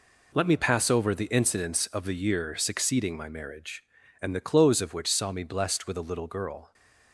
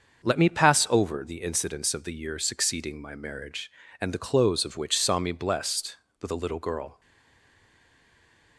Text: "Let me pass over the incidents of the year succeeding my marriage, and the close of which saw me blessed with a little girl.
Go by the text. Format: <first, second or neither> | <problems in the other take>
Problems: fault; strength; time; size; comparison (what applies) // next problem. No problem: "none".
first | starts louder than the rest; until 1.2 s; 6.5 dB // stays silent after the last word; noticeable; from 7.0 s on; 1.5 s long